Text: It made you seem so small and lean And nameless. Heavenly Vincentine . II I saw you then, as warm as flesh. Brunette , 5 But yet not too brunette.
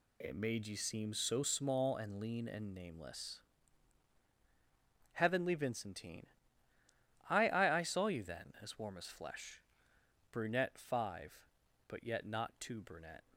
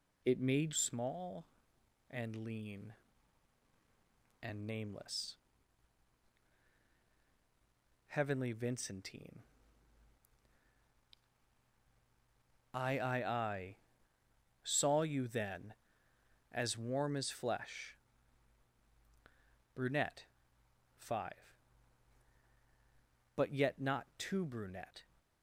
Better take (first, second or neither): first